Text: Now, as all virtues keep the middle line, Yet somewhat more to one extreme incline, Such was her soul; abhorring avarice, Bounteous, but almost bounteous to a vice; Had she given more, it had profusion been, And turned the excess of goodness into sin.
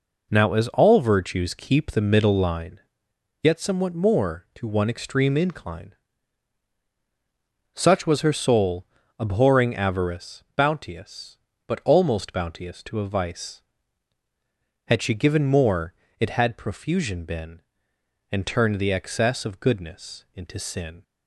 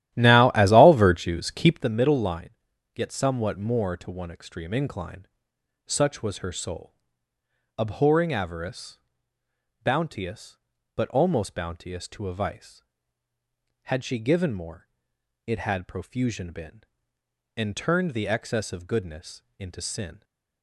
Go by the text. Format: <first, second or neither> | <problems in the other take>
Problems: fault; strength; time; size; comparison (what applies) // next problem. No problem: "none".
first | starts louder than the rest; strong; until 2.0 s; 13 dB // pauses between "goodness" and "into"; slight; at 19.4 s; 0.16 s long